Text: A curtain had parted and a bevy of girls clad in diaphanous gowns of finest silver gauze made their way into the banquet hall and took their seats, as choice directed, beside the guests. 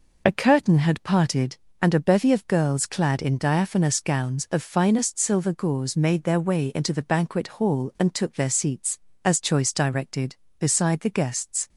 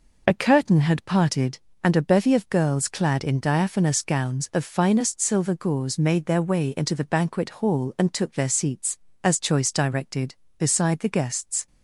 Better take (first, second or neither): neither